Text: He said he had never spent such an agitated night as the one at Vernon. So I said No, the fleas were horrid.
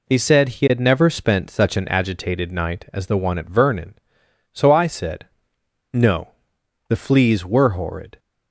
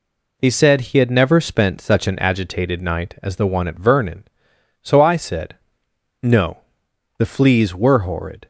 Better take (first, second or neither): neither